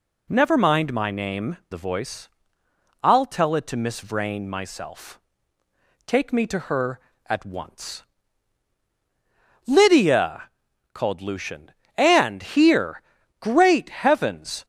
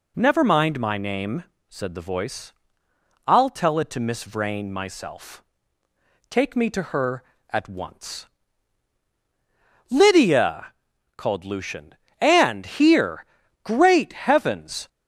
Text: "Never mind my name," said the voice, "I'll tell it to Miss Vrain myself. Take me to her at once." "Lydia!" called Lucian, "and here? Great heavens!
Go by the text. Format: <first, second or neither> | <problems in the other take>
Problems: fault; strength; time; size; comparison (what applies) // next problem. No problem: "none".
second | skips "said"; at 1.6 s